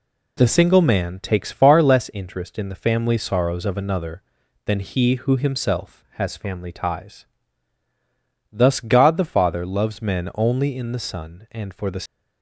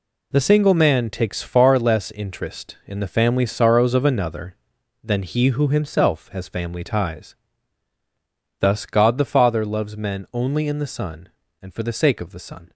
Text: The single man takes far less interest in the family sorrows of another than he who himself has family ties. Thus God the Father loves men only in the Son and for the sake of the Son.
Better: second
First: stops before "sake of the Son"; at 12.0 s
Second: none

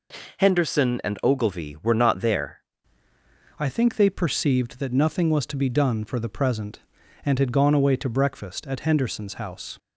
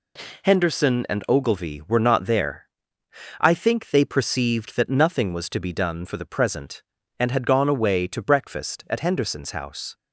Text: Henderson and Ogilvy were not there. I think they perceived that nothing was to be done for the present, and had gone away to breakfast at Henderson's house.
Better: second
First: changes voice at "I"; from 3.5 s on; 6.2 s long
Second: none

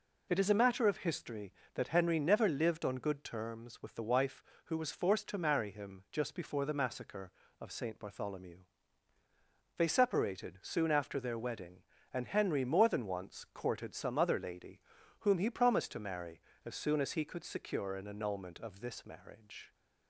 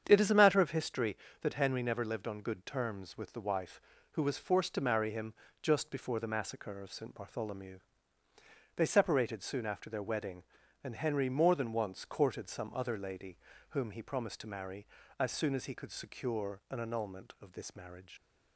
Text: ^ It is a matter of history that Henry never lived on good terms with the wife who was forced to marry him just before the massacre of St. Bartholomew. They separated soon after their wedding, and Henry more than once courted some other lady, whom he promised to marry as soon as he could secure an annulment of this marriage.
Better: first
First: none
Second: starts louder than the rest; strong; until 1.0 s; 8 dB // pauses between "him" and "just"; slight; at 5.3 s; 0.28 s long // leaves "marriage" unfinished; at 18.1 s; 80 ms

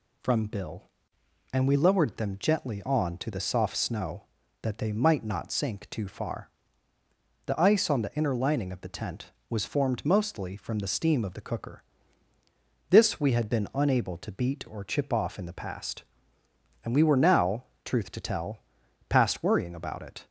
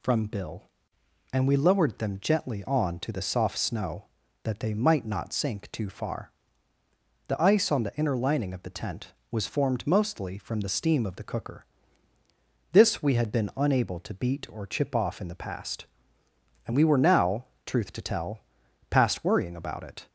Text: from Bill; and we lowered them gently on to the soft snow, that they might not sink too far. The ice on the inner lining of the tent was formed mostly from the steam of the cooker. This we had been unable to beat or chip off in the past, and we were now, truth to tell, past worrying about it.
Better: neither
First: none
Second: none

